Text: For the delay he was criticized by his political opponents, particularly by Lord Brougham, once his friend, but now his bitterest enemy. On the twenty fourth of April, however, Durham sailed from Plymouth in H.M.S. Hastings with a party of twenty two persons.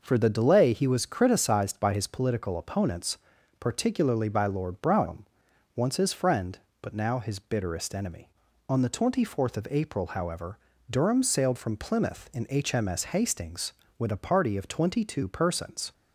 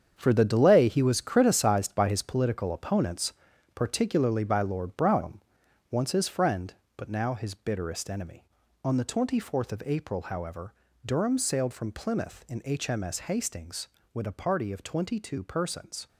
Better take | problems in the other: first | gets quieter; strong; throughout; 10 dB

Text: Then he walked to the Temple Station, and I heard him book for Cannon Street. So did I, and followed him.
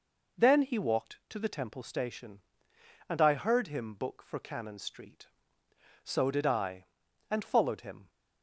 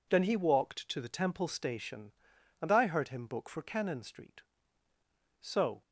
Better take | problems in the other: first | stops before "did I and followed him"; at 5.8 s

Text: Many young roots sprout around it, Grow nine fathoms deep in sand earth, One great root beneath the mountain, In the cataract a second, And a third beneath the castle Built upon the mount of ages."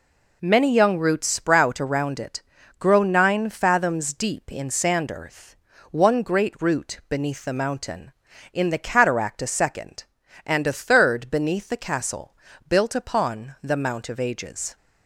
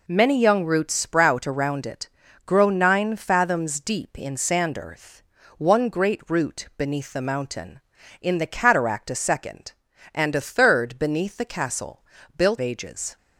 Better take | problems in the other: first | pauses between "castle" and "Built"; slight; at 12.0 s; 0.32 s long; slight in the first // skips "upon the mount of"; at 12.5 s

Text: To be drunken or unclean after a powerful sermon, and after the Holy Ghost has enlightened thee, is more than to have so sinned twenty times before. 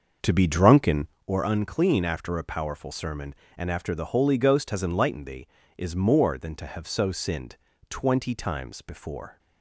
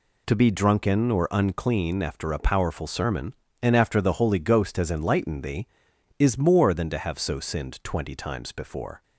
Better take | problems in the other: second | starts louder than the rest; until 1.2 s; 6.5 dB // pauses between "sinned" and "twenty"; slight; at 7.5 s; 0.32 s long

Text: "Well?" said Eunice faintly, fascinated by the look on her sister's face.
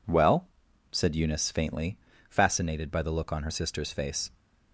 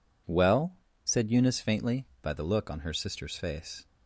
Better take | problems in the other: first | skips "fascinated"; at 2.1 s

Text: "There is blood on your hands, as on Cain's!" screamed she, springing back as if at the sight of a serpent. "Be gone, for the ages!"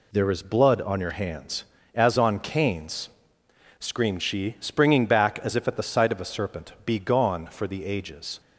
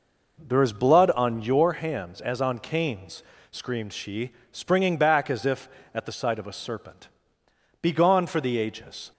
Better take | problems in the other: first | starts louder than the rest; noticeable; until 1.8 s; 5 dB

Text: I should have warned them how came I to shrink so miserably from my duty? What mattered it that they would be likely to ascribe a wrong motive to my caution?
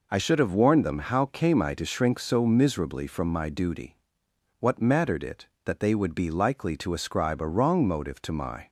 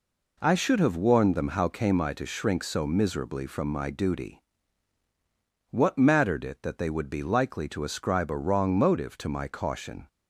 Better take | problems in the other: second | stops before "caution"; at 8.6 s

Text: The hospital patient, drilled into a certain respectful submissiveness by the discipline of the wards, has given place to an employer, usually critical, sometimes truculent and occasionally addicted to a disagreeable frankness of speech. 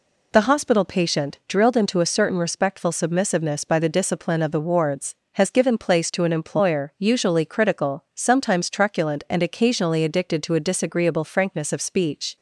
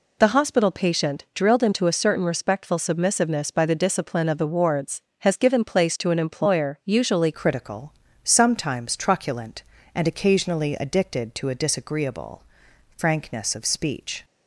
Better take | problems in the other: first | changes voice at "critical"; from 7.3 s on; 6.9 s long // pauses between "disagreeable" and "frankness"; noticeable; at 12.4 s; 0.54 s long

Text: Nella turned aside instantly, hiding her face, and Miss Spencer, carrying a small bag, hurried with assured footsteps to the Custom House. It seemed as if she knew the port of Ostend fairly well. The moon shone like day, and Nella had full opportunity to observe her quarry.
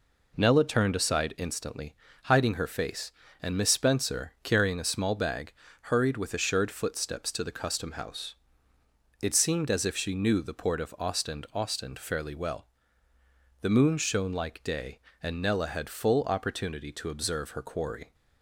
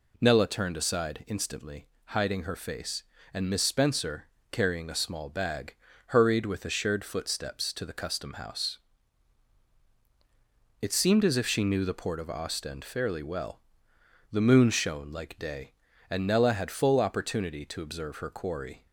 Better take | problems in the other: second | says "Ostend" twice; at 11.5 s

